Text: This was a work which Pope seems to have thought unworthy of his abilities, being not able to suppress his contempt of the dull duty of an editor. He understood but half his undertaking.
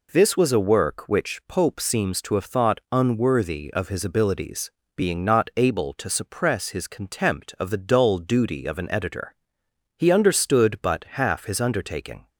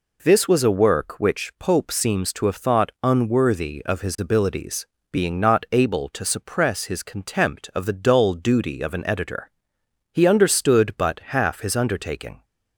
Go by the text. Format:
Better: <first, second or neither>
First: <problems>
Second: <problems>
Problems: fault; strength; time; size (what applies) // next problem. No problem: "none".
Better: neither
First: pauses between "but" and "half"; slight; at 11.0 s; 0.16 s long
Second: pauses between "but" and "half"; slight; at 11.1 s; 0.16 s long